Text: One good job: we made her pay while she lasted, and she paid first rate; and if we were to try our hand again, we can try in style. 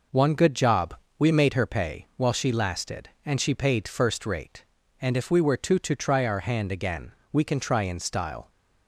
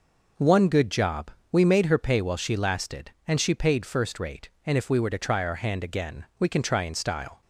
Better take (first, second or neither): second